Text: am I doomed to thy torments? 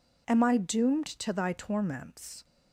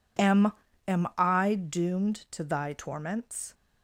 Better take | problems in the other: first | says "am" twice; at 0.8 s

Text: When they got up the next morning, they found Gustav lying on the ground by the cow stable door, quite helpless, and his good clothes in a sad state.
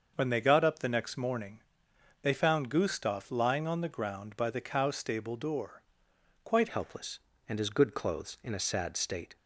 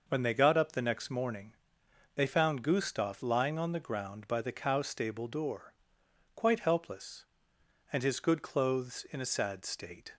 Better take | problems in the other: second | starts louder than the rest; until 1.1 s; 6.5 dB // changes voice at "helpless"; from 6.7 s on; 2.6 s long

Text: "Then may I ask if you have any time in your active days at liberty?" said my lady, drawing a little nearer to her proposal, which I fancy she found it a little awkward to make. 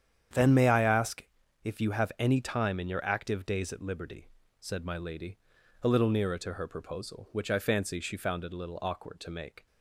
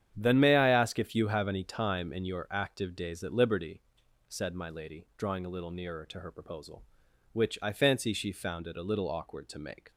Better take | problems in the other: second | starts louder than the rest; strong; until 1.7 s; 9 dB; strong in the second // pauses between "ask" and "if"; at 1.2 s; 0.38 s long // skips "drawing"; at 5.5 s

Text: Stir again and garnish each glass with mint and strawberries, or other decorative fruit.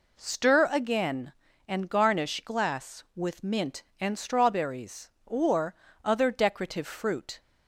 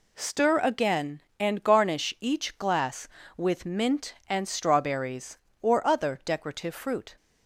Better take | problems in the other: second | skips "each"; at 2.4 s // pauses between "or" and "other"; slight; at 5.7 s; 0.30 s long

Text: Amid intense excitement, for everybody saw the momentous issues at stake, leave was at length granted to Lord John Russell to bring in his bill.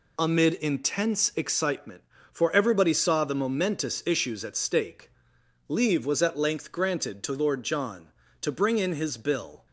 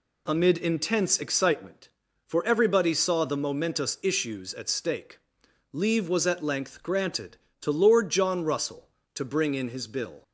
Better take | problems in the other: second | skips "Russell"; at 8.2 s

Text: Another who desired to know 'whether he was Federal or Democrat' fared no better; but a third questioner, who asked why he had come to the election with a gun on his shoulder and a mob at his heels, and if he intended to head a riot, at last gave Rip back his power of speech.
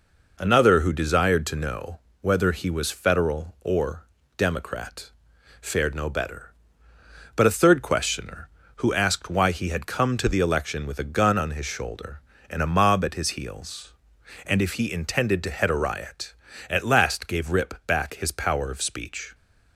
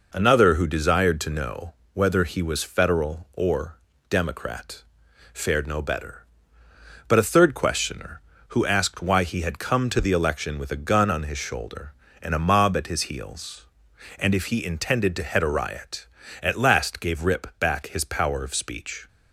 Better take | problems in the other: neither | pauses between "know" and "whether"; slight; the same in both // pauses between "or" and "Democrat"; slight; the same in both // pauses between "Democrat" and "fared"; noticeable; the same in both

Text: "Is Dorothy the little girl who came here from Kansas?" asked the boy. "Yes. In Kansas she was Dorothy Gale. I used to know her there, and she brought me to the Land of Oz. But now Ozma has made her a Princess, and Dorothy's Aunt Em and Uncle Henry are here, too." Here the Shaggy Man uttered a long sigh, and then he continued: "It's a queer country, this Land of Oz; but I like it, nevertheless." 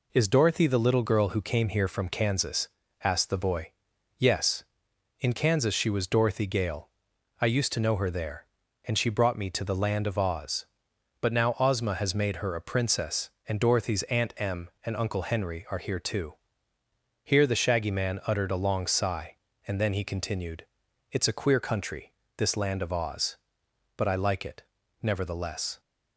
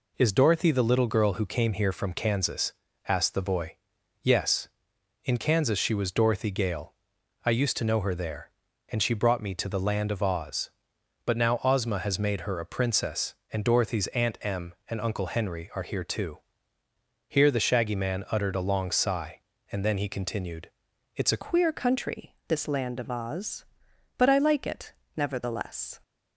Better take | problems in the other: first | changes voice at "queer"; from 21.4 s on; 4.5 s long

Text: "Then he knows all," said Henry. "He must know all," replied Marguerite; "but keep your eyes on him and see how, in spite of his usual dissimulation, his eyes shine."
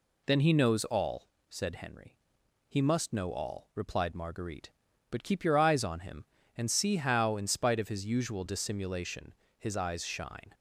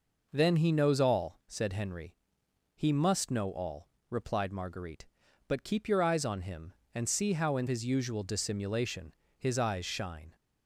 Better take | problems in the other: first | skips "spite of"; at 7.6 s

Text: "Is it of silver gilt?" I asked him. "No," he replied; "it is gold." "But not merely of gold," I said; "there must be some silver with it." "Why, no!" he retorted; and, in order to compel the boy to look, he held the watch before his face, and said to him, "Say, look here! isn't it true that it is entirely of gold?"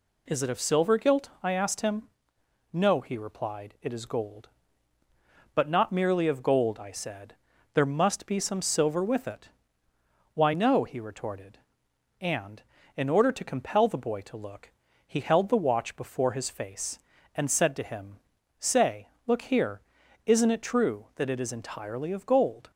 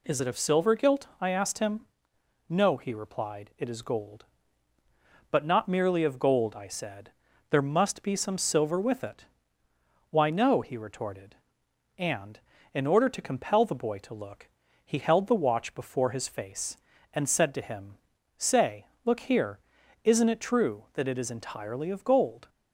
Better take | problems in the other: neither | none

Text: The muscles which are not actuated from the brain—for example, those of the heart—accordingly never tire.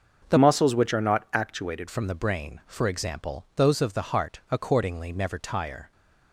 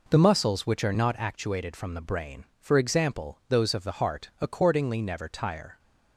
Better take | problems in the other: second | starts louder than the rest; until 1.3 s; 6.5 dB // changes voice from "muscles" to "actuated"; from 0.3 to 1.8 s; 1.5 s long

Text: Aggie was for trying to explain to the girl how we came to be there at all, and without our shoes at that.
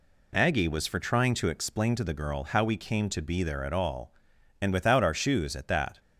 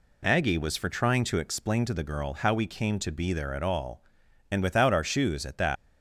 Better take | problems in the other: first | leaves "that" unfinished; at 5.7 s; 145 ms

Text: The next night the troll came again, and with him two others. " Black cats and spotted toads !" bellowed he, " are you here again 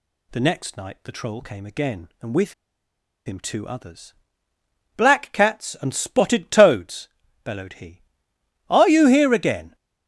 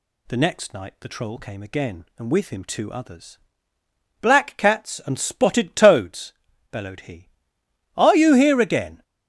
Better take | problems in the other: second | pauses between "with" and "him"; noticeable; at 2.5 s; 0.73 s long

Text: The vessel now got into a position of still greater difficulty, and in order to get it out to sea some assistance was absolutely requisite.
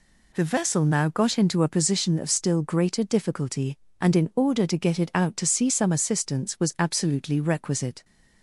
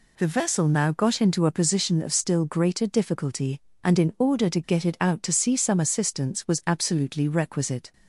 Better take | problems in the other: neither | none

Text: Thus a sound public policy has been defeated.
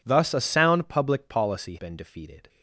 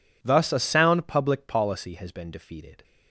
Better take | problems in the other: second | skips "has"; at 1.7 s

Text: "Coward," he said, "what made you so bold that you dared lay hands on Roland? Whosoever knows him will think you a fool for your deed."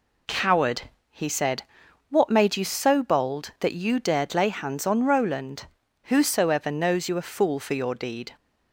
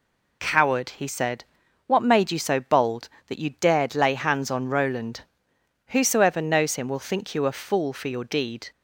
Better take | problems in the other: second | skips "him will think"; at 7.0 s

